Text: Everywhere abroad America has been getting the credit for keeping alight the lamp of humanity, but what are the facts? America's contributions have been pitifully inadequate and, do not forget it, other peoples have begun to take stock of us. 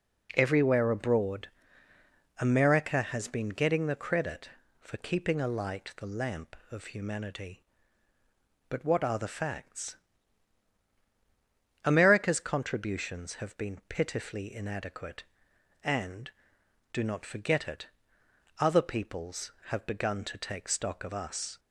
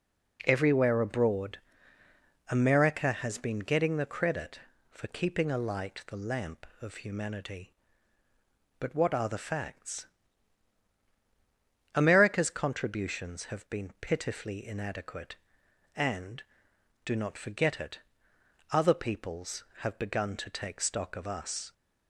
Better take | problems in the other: neither | pauses between "abroad" and "America"; noticeable; the same in both

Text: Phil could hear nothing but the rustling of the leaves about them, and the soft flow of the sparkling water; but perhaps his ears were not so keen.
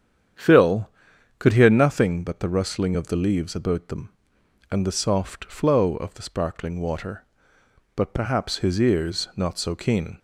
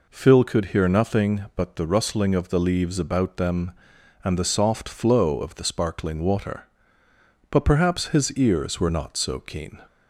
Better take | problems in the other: second | starts louder than the rest; strong; until 1.8 s; 9 dB // skips "were"; at 9.3 s

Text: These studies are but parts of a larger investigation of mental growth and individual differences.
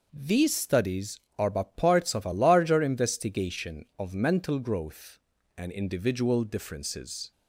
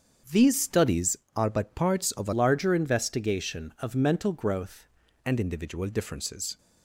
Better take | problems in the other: first | starts louder than the rest; strong; until 1.5 s; 7.5 dB // changes voice from "larger" to "growth"; from 2.3 to 4.8 s; 2.5 s long

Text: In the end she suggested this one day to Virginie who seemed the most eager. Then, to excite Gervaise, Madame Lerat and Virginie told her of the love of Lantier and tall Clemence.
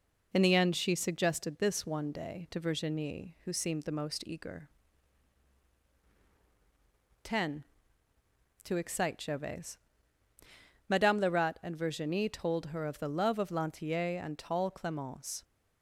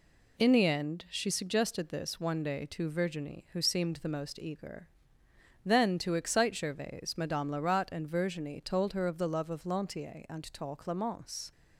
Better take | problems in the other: second | says "Ten" for "Then"; at 7.2 s

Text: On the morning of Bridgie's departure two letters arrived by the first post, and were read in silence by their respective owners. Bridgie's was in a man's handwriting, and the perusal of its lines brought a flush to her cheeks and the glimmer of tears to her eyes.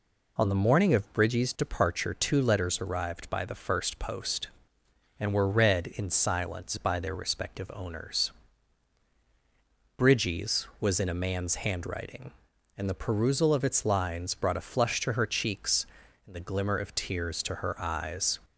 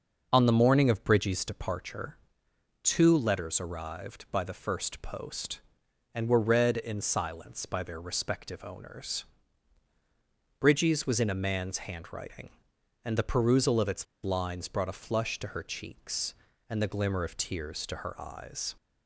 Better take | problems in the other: first | starts louder than the rest; until 1.3 s; 6.5 dB // pauses between "departure" and "two"; noticeable; at 2.1 s; 0.64 s long // pauses between "its" and "lines"; slight; at 14.0 s; 0.18 s long

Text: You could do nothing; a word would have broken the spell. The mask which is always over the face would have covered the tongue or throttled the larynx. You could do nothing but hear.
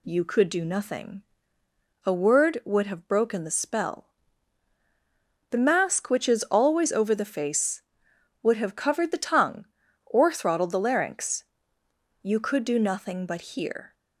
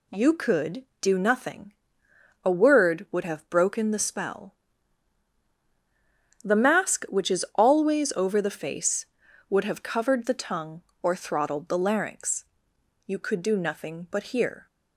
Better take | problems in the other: neither | none

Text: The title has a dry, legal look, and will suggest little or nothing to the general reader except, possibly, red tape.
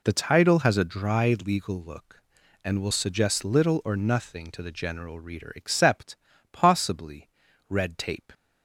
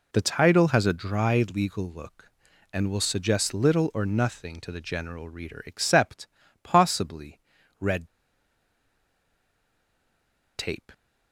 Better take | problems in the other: first | pauses between "red" and "tape"; strong; at 8.0 s; 2.4 s long

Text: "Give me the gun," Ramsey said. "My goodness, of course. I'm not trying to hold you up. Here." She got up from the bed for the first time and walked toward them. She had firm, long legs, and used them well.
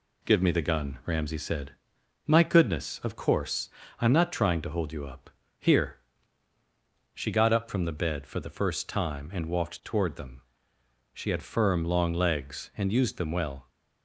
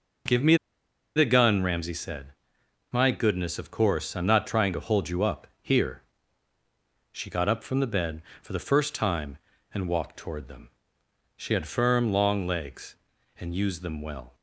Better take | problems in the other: first | pauses between "me" and "the"; noticeable; at 0.5 s; 0.59 s long

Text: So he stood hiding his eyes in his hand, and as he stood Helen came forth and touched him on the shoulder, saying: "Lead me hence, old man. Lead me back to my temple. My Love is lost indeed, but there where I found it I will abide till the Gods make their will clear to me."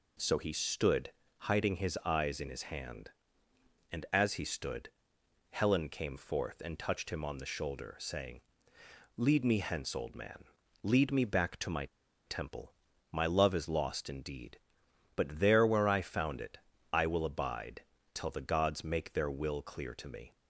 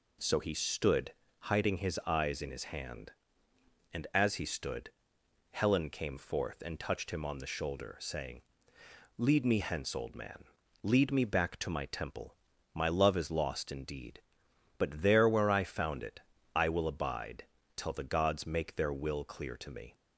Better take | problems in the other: second | pauses between "stood" and "hiding"; slight; at 1.1 s; 0.30 s long; slight in the second // pauses between "stood" and "Helen"; noticeable; at 4.8 s; 0.60 s long; noticeable in the second // pauses between "my" and "temple"; at 11.8 s; 0.39 s long // pauses between "it" and "I"; slight; at 16.5 s; 0.34 s long; slight in the second // pauses between "abide" and "till"; slight; at 17.8 s; 0.32 s long; slight in the second

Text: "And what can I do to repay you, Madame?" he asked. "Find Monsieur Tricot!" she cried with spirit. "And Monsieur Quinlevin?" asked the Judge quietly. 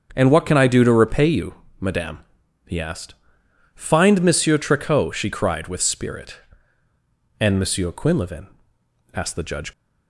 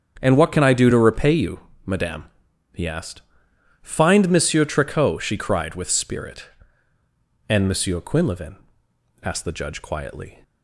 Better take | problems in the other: second | starts louder than the rest; until 1.1 s; 7 dB; strong in the second // stops before "quietly"; at 9.7 s

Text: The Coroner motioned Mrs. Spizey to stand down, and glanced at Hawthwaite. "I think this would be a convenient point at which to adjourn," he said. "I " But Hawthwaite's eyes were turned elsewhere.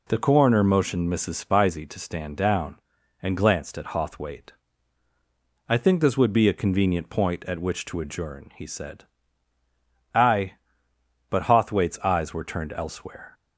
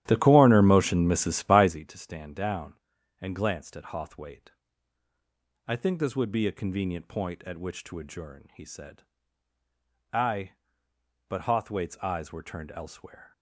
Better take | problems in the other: first | starts louder than the rest; strong; until 1.9 s; 13 dB

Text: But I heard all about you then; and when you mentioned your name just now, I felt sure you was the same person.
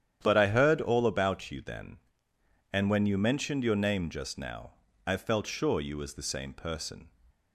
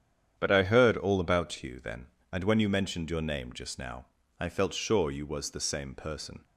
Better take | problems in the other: neither | starts louder than the rest; strong; the same in both

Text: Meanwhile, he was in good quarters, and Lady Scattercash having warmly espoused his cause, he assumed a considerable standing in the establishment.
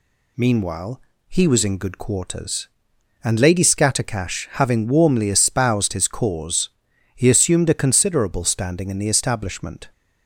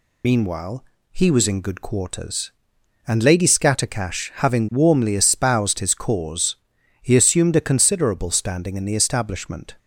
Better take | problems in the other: first | loses the start of "Meanwhile"; at 0.2 s; 50 ms

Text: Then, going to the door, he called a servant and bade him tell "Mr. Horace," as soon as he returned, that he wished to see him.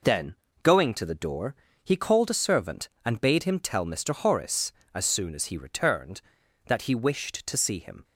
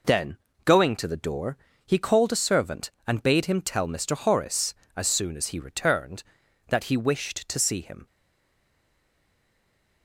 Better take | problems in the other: first | stays silent after the last word; noticeable; from 8.0 s on; 2.0 s long

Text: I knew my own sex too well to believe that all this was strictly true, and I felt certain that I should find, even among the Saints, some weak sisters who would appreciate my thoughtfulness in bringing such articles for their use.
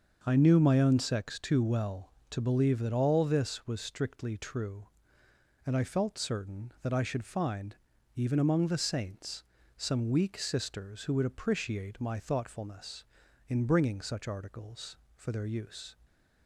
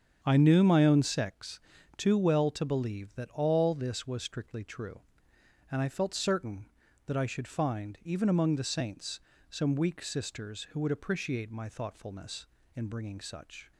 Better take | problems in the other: first | starts louder than the rest; strong; until 1.2 s; 7.5 dB; also in the first // pauses between "sex" and "too"; at 1.5 s; 0.38 s long // stops before "articles for their use"; at 13.7 s

